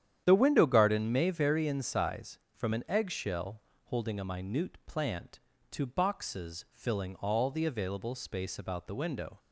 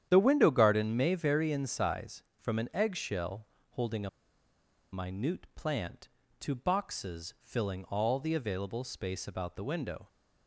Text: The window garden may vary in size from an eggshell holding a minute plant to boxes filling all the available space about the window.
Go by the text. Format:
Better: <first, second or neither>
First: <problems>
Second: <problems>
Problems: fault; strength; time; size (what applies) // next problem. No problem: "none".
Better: first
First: starts louder than the rest; strong; until 1.2 s; 9.5 dB // pauses between "eggshell" and "holding"; slight; at 3.6 s; 0.23 s long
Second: starts louder than the rest; strong; until 1.1 s; 9.5 dB // pauses between "eggshell" and "holding"; slight; at 3.4 s; 0.24 s long // pauses between "a" and "minute"; noticeable; at 4.0 s; 0.84 s long